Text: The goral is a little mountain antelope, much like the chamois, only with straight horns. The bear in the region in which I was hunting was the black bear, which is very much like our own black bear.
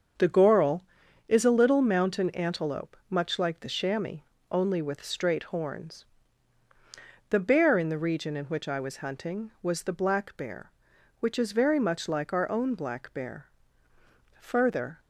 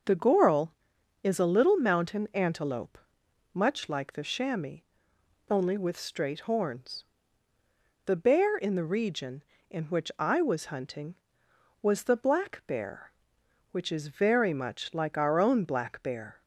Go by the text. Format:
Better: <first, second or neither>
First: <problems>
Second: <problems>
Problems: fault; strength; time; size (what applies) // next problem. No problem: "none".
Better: second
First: starts louder than the rest; strong; until 1.6 s; 7 dB // goes on to say "Further"; from 14.3 s on; 0.60 s long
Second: none